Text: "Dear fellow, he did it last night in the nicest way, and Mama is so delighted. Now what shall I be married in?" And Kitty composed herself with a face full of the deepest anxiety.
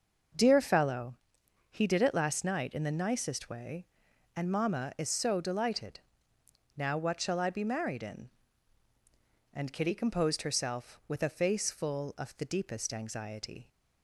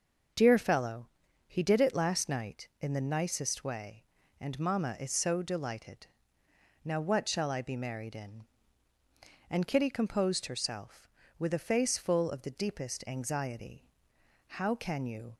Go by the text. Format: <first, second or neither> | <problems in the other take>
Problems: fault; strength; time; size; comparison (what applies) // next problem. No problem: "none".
first | starts louder than the rest; until 1.7 s; 6.5 dB; also in the first // goes on to say "How can you"; noticeable; from 14.4 s on; 0.90 s long